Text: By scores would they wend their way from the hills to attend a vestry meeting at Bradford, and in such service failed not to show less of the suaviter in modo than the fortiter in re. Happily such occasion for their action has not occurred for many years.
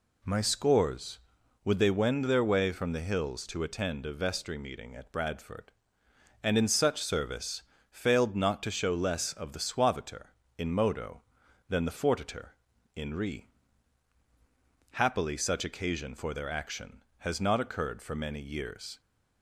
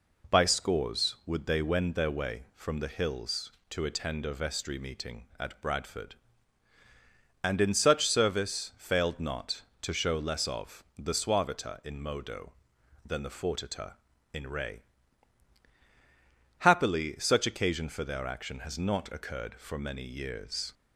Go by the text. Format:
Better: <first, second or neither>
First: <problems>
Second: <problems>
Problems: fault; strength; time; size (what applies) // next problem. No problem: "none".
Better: second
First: says "My" for "By"; at 0.2 s // pauses between "service" and "failed"; slight; at 7.6 s; 0.28 s long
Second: none